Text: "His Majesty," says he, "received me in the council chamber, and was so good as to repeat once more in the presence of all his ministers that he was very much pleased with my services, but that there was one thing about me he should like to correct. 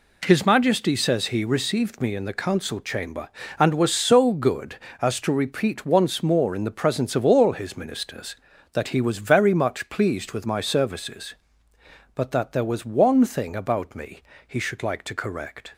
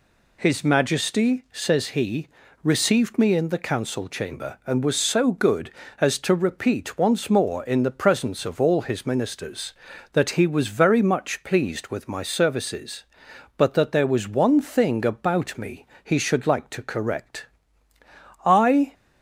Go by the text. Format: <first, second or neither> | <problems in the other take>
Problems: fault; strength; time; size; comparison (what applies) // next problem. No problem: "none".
first | pauses between "me" and "he"; slight; at 15.8 s; 0.20 s long; slight in the first // goes on to say "I"; slight; from 18.4 s on; 0.48 s long